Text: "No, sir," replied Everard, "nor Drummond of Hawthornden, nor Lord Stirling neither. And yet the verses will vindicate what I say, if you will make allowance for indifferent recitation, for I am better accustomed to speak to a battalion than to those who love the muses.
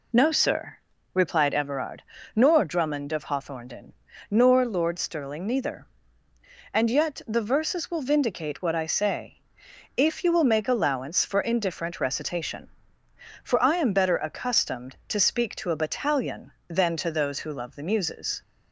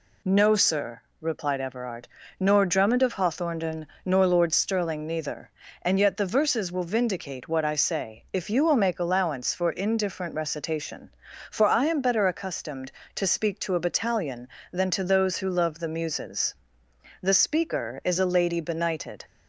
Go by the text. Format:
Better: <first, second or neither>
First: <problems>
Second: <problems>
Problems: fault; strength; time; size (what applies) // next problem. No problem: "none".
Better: first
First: none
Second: goes on to say "The speaker is a lady benighted"; strong; from 17.2 s on; 2.0 s long